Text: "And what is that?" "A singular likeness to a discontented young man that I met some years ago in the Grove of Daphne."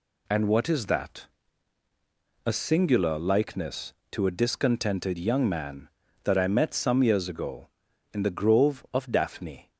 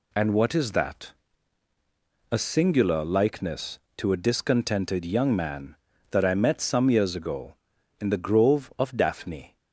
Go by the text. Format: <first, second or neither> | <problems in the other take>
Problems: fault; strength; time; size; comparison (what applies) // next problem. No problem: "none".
neither | none